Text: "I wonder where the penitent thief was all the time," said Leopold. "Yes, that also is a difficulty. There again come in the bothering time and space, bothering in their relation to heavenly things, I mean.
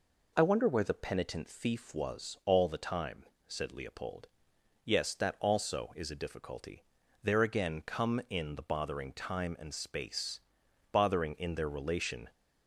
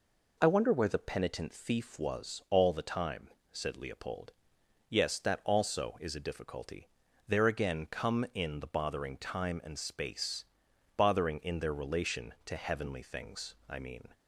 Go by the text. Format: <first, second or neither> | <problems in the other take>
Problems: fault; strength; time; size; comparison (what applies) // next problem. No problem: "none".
second | stops before "to heavenly things I mean"; at 12.3 s